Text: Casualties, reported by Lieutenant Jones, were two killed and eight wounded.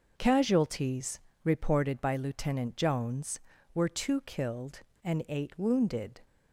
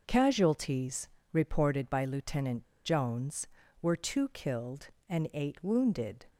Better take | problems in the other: first | pauses between "Lieutenant" and "Jones"; slight; at 2.6 s; 0.19 s long

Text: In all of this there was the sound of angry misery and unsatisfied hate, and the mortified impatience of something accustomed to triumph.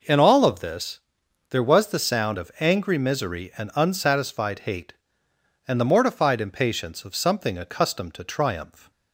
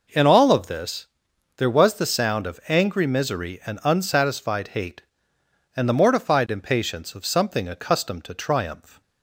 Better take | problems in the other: neither | pauses between "this" and "there"; noticeable; the same in both

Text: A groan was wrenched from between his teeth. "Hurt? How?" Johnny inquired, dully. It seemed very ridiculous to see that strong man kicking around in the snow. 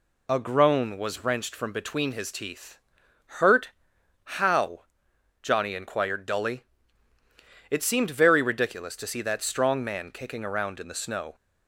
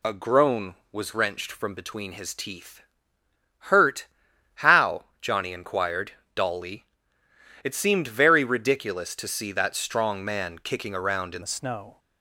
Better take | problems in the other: first | changes voice at "the"; from 11.4 s on; 0.5 s long

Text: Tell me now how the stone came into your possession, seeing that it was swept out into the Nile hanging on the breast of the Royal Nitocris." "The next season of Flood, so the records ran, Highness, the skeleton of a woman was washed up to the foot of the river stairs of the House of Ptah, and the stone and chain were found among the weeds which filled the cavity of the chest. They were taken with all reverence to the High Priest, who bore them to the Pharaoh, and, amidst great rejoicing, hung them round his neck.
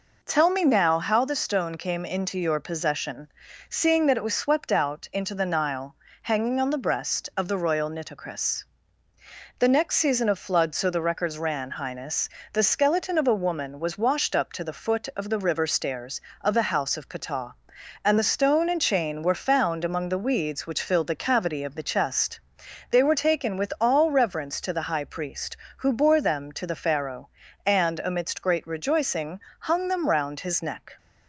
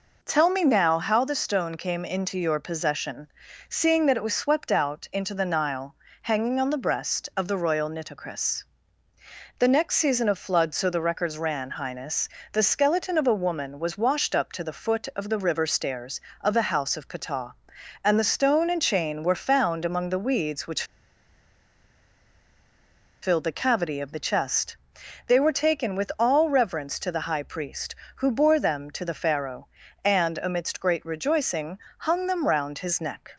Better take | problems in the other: first | pauses between "Nile" and "hanging"; slight; at 5.9 s; 0.28 s long; slight in the first // pauses between "which" and "filled"; strong; at 20.8 s; 2.3 s long

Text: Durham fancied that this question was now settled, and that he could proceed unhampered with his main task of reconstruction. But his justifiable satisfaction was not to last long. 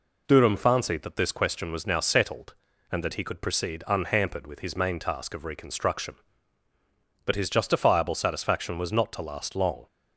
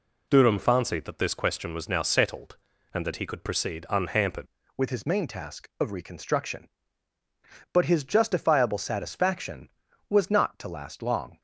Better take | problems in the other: first | changes voice at "with"; from 4.7 s on; 6.6 s long

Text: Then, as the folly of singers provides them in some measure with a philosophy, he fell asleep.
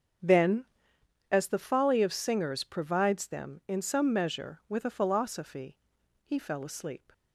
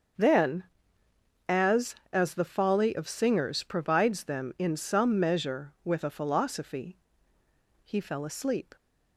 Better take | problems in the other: first | starts louder than the rest; until 2.1 s; 6.5 dB; also in the first // says "as" twice; at 2.1 s

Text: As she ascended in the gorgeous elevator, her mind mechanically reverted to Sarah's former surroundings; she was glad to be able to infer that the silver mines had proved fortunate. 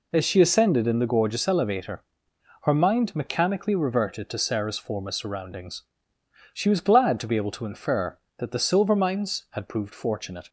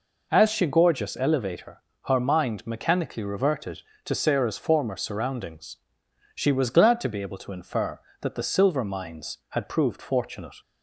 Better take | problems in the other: first | skips "ascended in the"; at 0.6 s

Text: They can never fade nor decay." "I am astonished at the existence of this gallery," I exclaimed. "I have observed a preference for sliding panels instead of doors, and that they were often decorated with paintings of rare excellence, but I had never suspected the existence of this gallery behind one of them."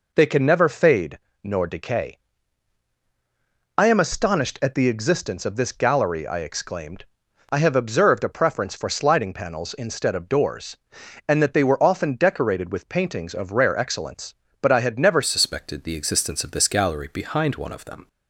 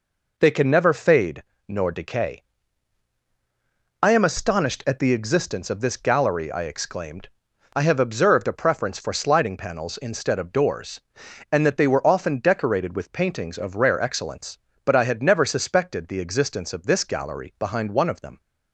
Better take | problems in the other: second | pauses between "fade" and "nor"; slight; at 1.1 s; 0.26 s long; slight in the second // changes voice at "suspected"; from 15.2 s on; 2.8 s long

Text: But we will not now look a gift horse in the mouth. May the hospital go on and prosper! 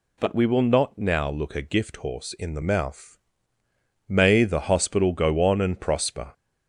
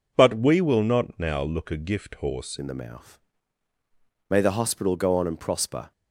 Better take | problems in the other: first | changes voice at "in"; from 2.5 s on; 3.4 s long

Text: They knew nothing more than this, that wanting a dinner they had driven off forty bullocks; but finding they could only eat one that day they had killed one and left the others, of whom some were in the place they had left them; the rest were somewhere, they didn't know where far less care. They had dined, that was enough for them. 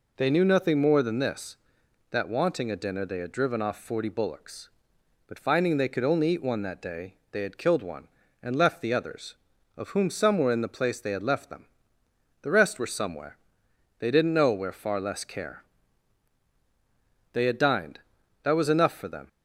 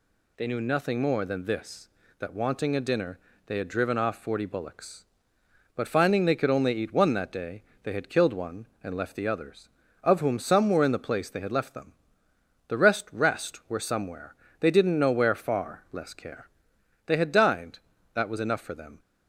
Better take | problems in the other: first | pauses between "dinner" and "they"; slight; at 3.1 s; 0.28 s long // pauses between "day" and "they"; slight; at 7.6 s; 0.22 s long; slight in the first // says "rest" twice; at 13.1 s

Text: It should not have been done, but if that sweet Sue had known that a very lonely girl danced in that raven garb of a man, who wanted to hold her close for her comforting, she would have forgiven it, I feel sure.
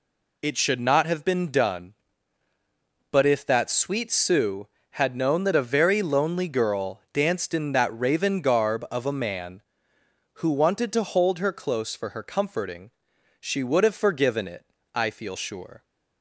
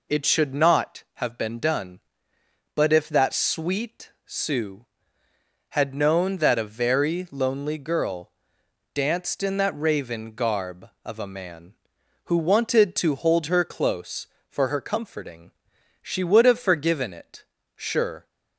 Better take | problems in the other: first | pauses between "girl" and "danced"; noticeable; at 8.2 s; 0.64 s long // skips "I feel"; at 17.5 s

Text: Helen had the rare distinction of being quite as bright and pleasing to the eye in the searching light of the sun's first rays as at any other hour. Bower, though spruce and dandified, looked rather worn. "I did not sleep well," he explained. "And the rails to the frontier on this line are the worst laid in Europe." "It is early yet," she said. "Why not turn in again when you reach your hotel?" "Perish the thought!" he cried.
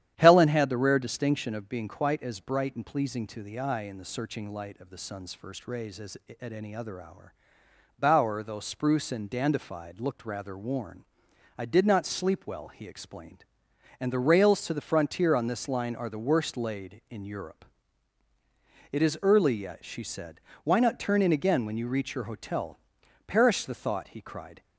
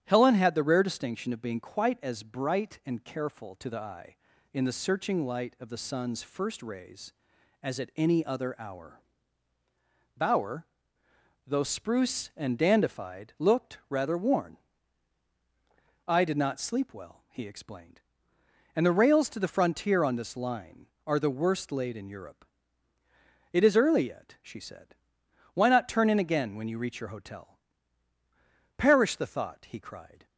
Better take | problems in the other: first | starts louder than the rest; strong; until 1.0 s; 9.5 dB; strong in the first // says "careful" for "pleasing"; at 3.0 s

